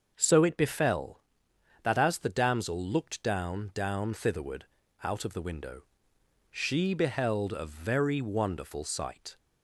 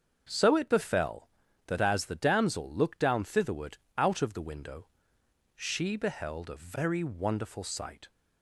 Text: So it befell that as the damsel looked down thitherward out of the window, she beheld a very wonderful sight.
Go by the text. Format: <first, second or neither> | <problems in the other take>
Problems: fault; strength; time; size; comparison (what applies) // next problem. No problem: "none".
second | starts louder than the rest; until 1.1 s; 6.5 dB; also in the second // says "down" twice; at 3.7 s // pauses between "thitherward" and "out"; at 4.6 s; 0.38 s long; slight in the second